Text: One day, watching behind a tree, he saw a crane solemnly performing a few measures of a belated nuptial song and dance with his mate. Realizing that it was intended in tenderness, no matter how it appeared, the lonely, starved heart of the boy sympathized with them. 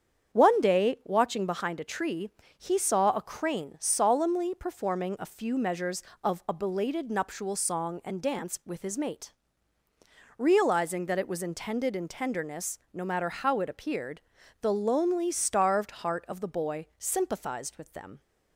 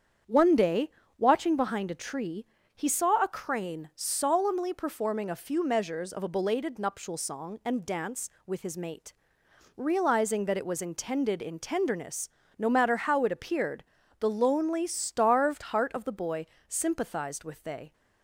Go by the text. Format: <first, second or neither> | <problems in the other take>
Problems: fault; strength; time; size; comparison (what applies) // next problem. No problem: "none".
first | starts louder than the rest; strong; until 1.5 s; 8 dB; strong in the first // pauses between "boy" and "sympathized"; slight; at 16.4 s; 0.22 s long // says "they" for "them"; at 17.6 s